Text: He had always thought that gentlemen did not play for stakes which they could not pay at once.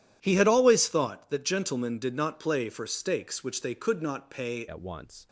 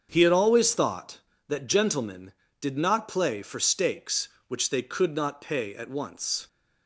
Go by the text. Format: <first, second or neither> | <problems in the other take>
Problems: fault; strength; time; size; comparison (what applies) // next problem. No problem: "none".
second | starts louder than the rest; strong; until 1.2 s; 11.5 dB; strong in the second // changes voice at "at"; from 4.6 s on; 0.6 s long